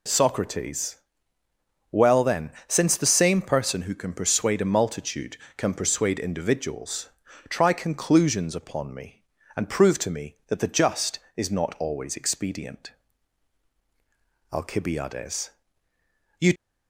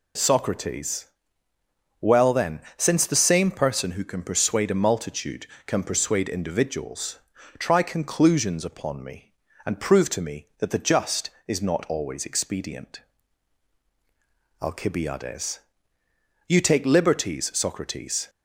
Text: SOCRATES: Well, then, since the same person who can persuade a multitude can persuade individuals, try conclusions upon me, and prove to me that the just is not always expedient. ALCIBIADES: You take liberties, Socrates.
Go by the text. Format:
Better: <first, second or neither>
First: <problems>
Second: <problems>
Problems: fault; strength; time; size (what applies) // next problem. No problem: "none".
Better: second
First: stops before "take liberties Socrates"; at 16.5 s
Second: none